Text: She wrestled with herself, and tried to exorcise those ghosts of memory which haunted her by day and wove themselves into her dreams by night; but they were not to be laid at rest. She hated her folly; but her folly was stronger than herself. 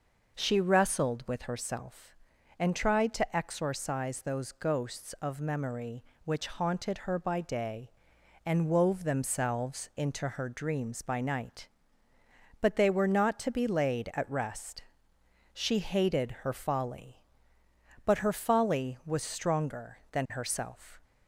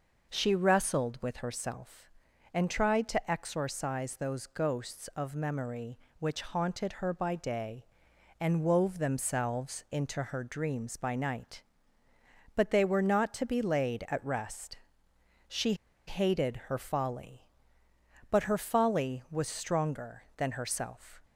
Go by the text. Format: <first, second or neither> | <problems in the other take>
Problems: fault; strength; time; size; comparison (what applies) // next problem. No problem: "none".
first | pauses between "She" and "hated"; slight; at 15.7 s; 0.33 s long